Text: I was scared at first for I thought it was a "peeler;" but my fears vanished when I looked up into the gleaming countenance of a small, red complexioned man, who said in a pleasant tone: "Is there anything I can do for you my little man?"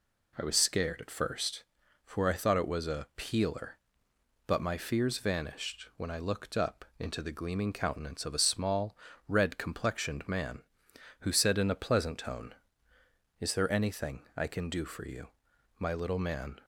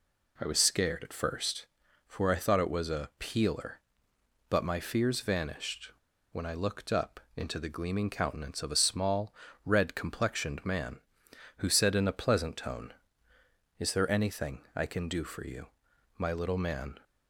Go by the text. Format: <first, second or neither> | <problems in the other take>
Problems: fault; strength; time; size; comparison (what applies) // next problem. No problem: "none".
first | pauses between "vanished" and "when"; at 5.9 s; 0.39 s long // pauses between "up" and "into"; slight; at 7.1 s; 0.16 s long // pauses between "you" and "my"; noticeable; at 15.6 s; 0.54 s long; noticeable in the first